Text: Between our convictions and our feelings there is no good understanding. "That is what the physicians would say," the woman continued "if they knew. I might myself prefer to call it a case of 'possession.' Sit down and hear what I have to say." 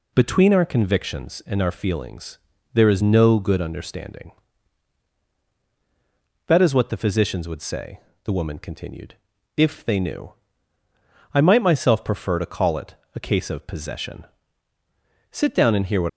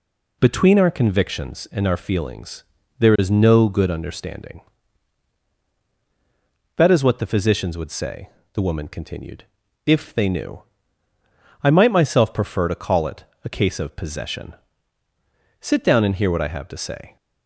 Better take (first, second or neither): second